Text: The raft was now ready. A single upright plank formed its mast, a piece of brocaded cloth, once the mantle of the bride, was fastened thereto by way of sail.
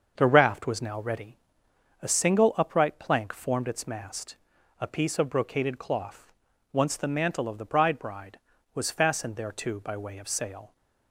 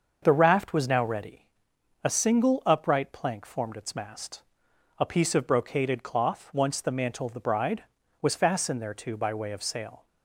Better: second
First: starts louder than the rest; until 1.1 s; 6.5 dB // says "bride" twice; at 7.9 s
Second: starts louder than the rest; until 1.2 s; 6.5 dB

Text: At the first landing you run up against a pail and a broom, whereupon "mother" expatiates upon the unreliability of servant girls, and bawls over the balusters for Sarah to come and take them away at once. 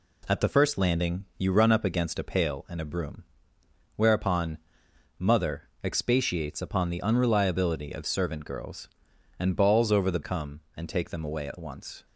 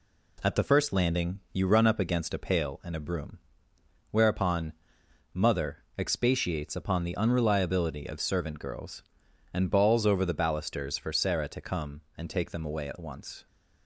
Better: second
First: pauses between "whereupon" and "mother"; noticeable; at 4.5 s; 0.62 s long // pauses between "mother" and "expatiates"; slight; at 5.6 s; 0.16 s long // skips "balusters for Sarah to"; at 10.2 s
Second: pauses between "whereupon" and "mother"; noticeable; at 4.7 s; 0.62 s long // pauses between "mother" and "expatiates"; slight; at 5.8 s; 0.15 s long

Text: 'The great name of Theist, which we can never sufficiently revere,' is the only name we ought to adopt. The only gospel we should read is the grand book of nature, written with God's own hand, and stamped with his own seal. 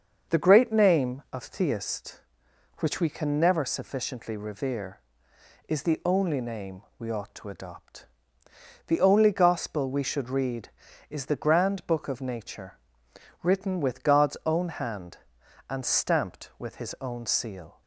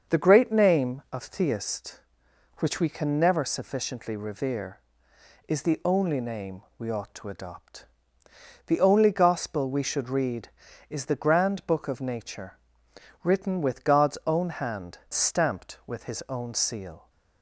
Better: first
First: starts louder than the rest; until 1.4 s; 6.5 dB // pauses between "name" and "we"; slight; at 6.8 s; 0.16 s long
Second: starts louder than the rest; until 1.2 s; 6.5 dB // pauses between "name" and "we"; slight; at 6.6 s; 0.16 s long // skips "and"; at 15.0 s

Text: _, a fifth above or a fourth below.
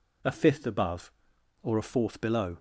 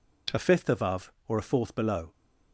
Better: neither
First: none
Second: none

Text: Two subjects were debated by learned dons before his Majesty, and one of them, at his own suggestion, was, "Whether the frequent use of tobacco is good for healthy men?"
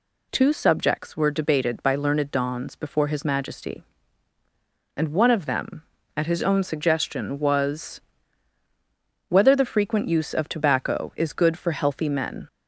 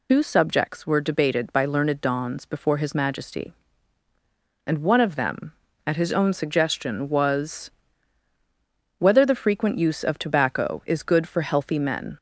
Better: first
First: none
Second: loses the start of "Two"; at 0.0 s; 90 ms

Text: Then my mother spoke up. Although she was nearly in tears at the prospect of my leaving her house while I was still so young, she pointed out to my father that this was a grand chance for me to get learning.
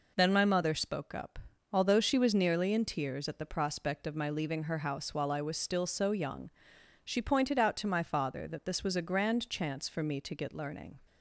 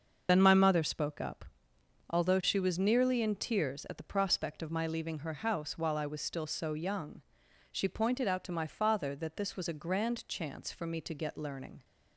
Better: first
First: none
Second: loses the start of "Then"; at 0.2 s; 50 ms // starts louder than the rest; until 1.3 s; 6.5 dB

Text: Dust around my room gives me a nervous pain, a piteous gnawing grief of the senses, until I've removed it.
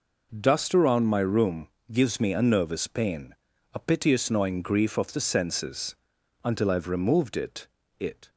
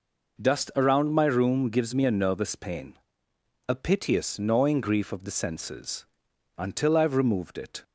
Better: second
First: pauses between "room" and "gives"; slight; at 1.6 s; 0.24 s long // says "it" twice; at 7.9 s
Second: none

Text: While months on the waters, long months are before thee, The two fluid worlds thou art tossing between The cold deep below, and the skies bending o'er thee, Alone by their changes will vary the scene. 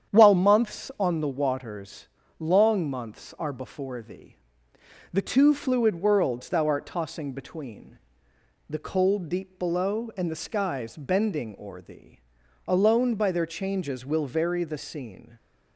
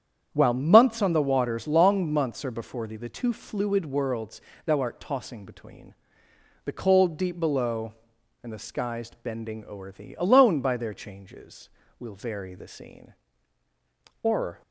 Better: first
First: starts louder than the rest; strong; until 1.1 s; 8.5 dB // pauses between "between" and "The"; noticeable; at 7.9 s; 0.72 s long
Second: starts louder than the rest; strong; until 1.3 s; 9 dB // pauses between "worlds" and "thou"; slight; at 4.3 s; 0.26 s long // pauses between "between" and "The"; noticeable; at 5.9 s; 0.70 s long // goes on to say "Or"; slight; from 14.2 s on; 0.38 s long

